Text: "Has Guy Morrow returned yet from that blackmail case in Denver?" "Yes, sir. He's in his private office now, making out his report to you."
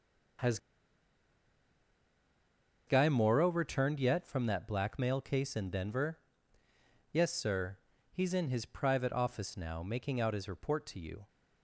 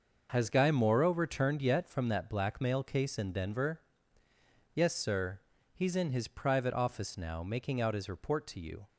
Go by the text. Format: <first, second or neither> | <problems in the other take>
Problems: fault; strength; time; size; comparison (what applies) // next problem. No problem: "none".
second | pauses between "Has" and "Guy"; strong; at 0.5 s; 2.2 s long